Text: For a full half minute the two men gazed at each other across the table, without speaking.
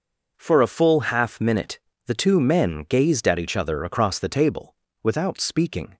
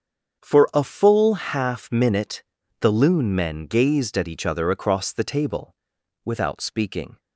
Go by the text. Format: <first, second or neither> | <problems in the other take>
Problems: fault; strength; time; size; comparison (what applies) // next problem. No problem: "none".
first | starts louder than the rest; strong; until 1.4 s; 7 dB // pauses between "minute" and "the"; at 2.4 s; 0.38 s long; slight in the first // says "loon" for "two"; at 2.9 s